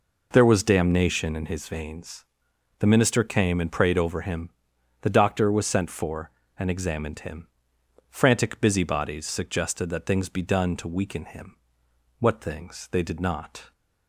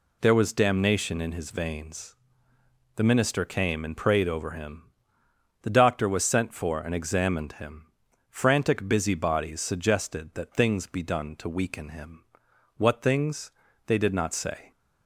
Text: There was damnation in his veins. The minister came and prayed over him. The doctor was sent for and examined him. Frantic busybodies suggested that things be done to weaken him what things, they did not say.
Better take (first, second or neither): second